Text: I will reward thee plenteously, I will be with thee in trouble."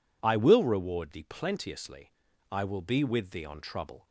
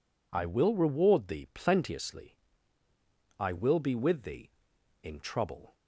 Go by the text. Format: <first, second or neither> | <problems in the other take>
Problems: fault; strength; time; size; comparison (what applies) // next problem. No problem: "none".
second | says "on" for "in"; at 3.4 s